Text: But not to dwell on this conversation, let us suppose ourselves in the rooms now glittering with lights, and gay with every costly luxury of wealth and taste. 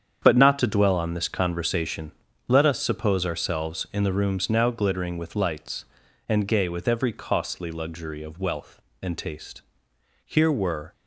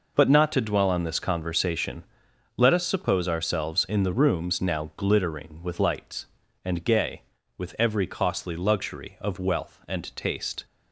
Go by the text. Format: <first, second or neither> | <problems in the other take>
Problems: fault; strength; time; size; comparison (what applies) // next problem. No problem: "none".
second | starts louder than the rest; strong; until 1.2 s; 8 dB // goes on to say "Here were"; noticeable; from 10.2 s on; 0.66 s long